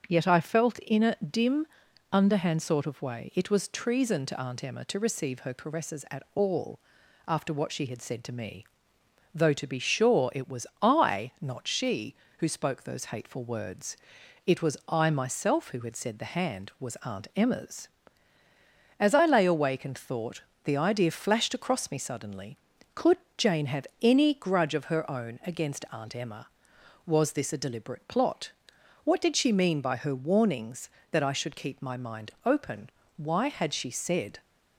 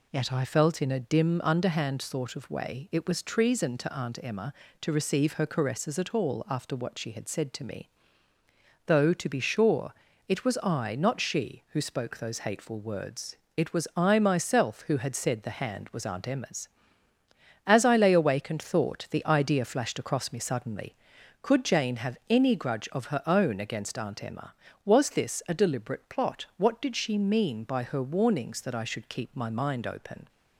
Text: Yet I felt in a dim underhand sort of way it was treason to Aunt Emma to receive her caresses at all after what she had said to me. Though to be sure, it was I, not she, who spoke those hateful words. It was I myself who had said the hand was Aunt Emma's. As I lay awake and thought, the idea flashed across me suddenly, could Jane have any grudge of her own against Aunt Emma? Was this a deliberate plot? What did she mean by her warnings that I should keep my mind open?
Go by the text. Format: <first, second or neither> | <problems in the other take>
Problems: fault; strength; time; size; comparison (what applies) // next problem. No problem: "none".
second | starts louder than the rest; until 1.0 s; 6.5 dB // pauses between "dim" and "underhand"; noticeable; at 1.6 s; 0.46 s long // pauses between "all" and "after"; noticeable; at 6.7 s; 0.48 s long // pauses between "was" and "I"; slight; at 10.6 s; 0.16 s long // pauses between "could" and "Jane"; slight; at 23.1 s; 0.20 s long // goes on to say "Why had she said"; noticeable; from 33.1 s on; 1.2 s long